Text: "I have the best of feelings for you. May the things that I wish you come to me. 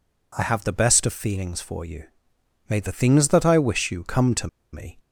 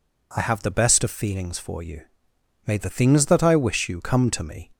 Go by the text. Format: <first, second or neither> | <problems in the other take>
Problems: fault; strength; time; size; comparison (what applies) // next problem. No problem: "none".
second | pauses between "to" and "me"; slight; at 4.4 s; 0.25 s long